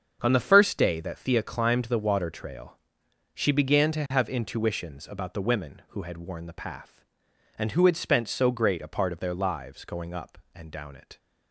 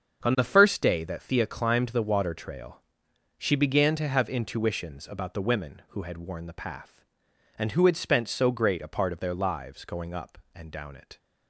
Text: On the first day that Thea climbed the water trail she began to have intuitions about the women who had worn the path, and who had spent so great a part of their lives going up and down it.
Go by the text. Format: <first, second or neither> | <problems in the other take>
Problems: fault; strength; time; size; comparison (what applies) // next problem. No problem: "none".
neither | starts louder than the rest; the same in both // pauses between "trail" and "she"; noticeable; the same in both